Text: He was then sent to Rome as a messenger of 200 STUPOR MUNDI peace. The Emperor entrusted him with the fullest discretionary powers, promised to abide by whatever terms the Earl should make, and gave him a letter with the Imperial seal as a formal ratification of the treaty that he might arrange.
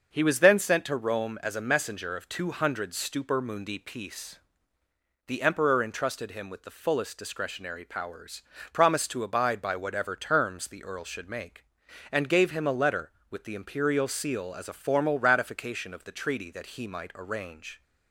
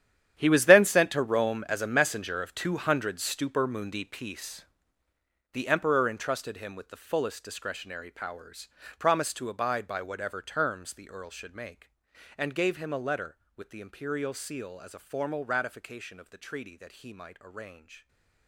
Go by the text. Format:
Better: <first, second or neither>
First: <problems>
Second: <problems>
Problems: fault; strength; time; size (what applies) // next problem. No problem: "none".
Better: first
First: starts louder than the rest; until 1.1 s; 6.5 dB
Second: gets quieter; strong; throughout; 15.5 dB // starts louder than the rest; strong; until 1.3 s; 10.5 dB // stays silent after the last word; slight; from 17.9 s on; 0.5 s long